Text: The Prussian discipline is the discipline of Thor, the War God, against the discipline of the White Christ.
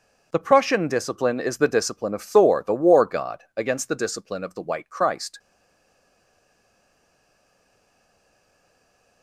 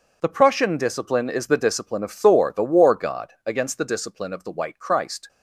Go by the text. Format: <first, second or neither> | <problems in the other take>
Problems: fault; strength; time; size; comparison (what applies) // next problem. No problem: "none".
second | stays silent after the last word; strong; from 5.3 s on; 3.9 s long